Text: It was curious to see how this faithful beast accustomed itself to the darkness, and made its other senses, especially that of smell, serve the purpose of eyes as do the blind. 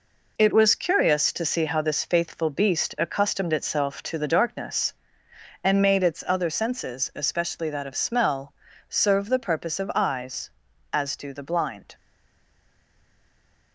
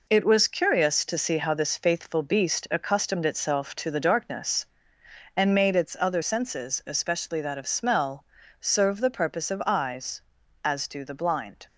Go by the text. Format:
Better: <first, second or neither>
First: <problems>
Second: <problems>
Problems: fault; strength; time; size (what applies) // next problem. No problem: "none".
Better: second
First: stays silent after the last word; noticeable; from 11.9 s on; 1.8 s long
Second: none